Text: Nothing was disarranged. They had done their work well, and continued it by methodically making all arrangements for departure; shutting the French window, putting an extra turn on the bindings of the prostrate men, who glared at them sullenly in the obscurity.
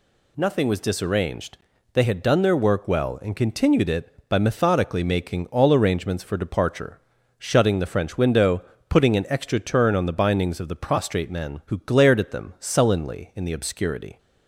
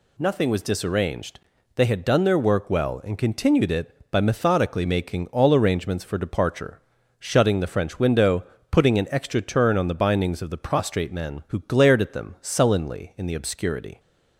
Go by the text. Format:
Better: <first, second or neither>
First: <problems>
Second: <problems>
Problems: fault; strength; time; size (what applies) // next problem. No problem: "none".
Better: neither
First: none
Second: none